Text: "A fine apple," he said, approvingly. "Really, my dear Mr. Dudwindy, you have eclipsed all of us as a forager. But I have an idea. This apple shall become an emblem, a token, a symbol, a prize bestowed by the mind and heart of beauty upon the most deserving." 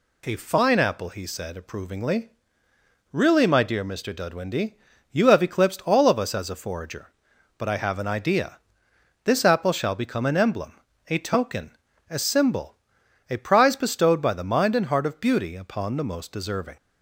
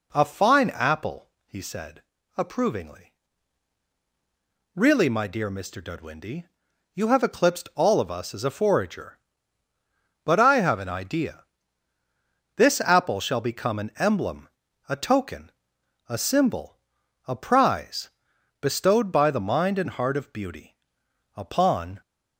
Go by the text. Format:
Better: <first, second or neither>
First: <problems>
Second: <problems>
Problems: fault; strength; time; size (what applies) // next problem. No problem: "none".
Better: first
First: none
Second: pauses between "prize" and "bestowed"; noticeable; at 18.0 s; 0.50 s long // pauses between "beauty" and "upon"; noticeable; at 20.7 s; 0.62 s long // stops before "the most deserving"; at 22.0 s